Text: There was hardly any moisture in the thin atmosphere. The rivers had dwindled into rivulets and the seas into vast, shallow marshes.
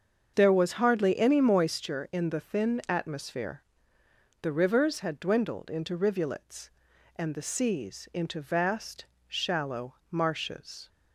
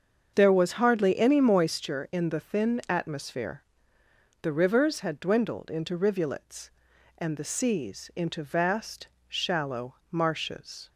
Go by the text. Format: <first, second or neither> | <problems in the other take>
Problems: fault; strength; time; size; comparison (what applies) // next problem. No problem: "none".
neither | starts louder than the rest; the same in both